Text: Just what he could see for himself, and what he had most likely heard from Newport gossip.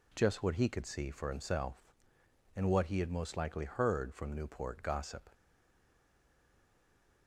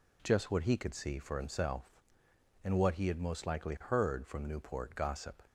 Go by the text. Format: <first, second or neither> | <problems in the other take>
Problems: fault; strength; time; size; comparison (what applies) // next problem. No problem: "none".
second | stays silent after the last word; noticeable; from 5.3 s on; 1.9 s long